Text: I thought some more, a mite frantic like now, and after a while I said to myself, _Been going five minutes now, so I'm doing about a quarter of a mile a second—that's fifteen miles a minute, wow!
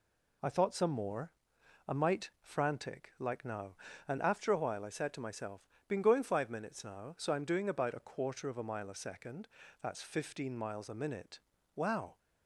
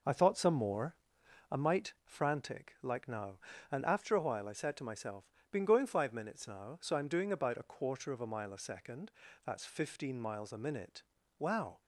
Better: first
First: none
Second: starts louder than the rest; noticeable; until 1.6 s; 5 dB

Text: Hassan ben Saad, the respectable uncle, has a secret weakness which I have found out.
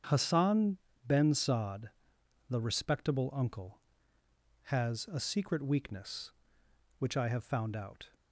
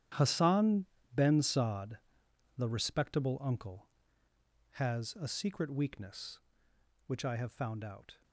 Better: first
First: starts louder than the rest; strong; until 1.3 s; 8 dB // pauses between "Hassan" and "ben"; slight; at 0.7 s; 0.30 s long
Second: gets quieter; strong; throughout; 15 dB // starts louder than the rest; strong; until 1.4 s; 11 dB // pauses between "Hassan" and "ben"; slight; at 0.8 s; 0.30 s long

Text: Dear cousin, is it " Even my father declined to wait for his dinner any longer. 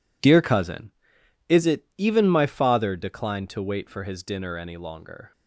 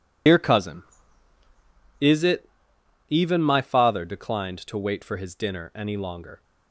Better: first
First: none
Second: loses the start of "Dear"; at 0.2 s; 75 ms

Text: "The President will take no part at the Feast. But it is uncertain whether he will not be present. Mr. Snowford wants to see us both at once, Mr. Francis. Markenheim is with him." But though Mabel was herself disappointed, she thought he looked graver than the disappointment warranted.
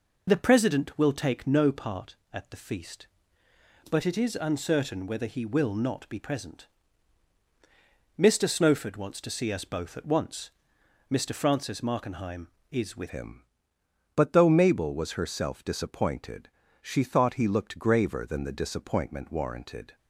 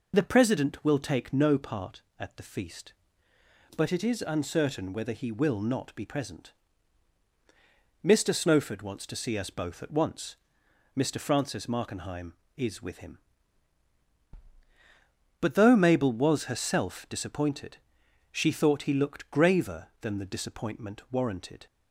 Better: second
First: changes voice at "him"; from 13.0 s on; 6.9 s long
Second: none

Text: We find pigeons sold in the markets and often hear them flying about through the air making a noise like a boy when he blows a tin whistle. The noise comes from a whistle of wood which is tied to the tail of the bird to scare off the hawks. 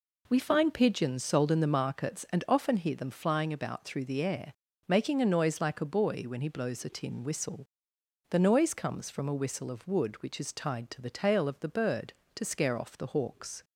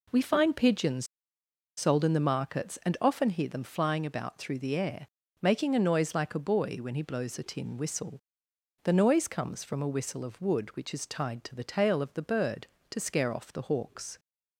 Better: first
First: pauses between "air" and "making"; slight; at 4.5 s; 0.34 s long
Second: pauses between "pigeons" and "sold"; noticeable; at 1.0 s; 0.72 s long // pauses between "air" and "making"; slight; at 5.0 s; 0.34 s long

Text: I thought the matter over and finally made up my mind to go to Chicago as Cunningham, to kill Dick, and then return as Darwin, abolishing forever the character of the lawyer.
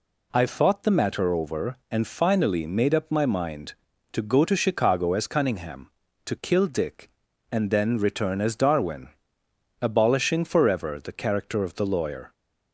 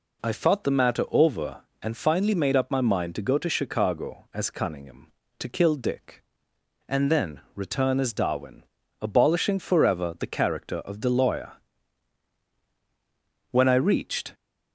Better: first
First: none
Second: goes on to say "When I reached"; noticeable; from 13.5 s on; 0.82 s long

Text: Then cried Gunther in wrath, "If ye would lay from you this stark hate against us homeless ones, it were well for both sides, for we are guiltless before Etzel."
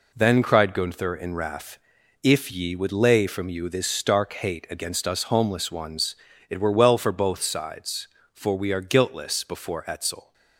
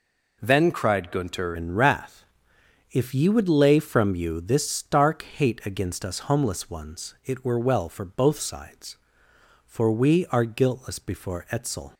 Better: first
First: none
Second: changes voice at "in"; from 1.5 s on; 10.4 s long

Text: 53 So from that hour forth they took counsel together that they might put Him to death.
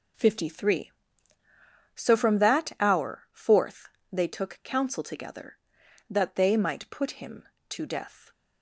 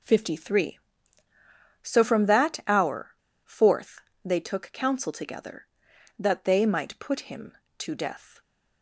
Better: first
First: pauses between "forth" and "they"; slight; at 3.8 s; 0.22 s long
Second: pauses between "hour" and "forth"; slight; at 3.1 s; 0.35 s long // pauses between "forth" and "they"; slight; at 4.0 s; 0.22 s long

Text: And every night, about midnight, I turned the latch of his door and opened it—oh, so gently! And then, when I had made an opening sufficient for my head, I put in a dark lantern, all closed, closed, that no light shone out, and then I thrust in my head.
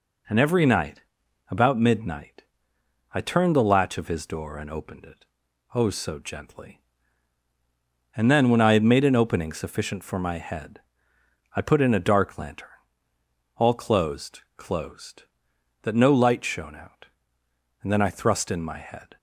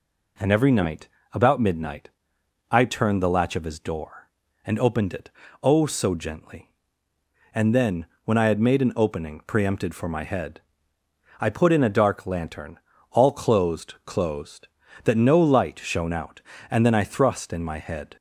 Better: first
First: none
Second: says "preempted" for "sufficient"; at 9.4 s

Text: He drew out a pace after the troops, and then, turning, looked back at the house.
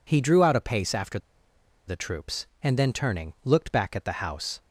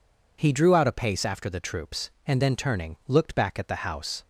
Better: second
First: pauses between "after" and "the"; noticeable; at 1.1 s; 0.69 s long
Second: none

